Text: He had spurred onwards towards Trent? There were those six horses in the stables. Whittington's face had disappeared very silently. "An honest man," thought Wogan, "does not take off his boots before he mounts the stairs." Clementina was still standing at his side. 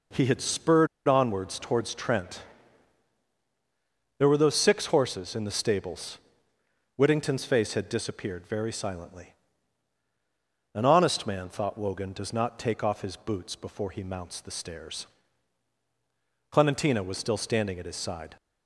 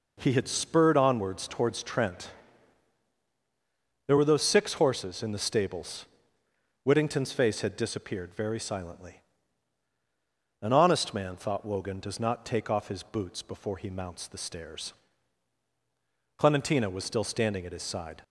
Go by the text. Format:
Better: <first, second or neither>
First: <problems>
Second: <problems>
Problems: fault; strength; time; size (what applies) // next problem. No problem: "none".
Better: second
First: pauses between "spurred" and "onwards"; slight; at 0.8 s; 0.20 s long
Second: none